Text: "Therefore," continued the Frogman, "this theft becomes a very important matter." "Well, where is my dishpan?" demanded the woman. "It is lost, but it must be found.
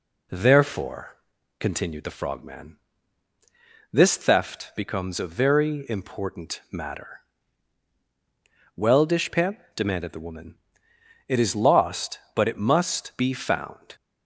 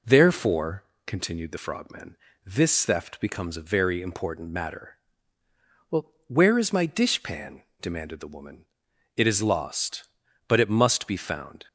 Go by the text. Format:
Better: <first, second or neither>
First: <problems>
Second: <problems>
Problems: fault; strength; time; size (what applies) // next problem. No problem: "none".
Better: second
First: skips "where is my"; at 9.0 s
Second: none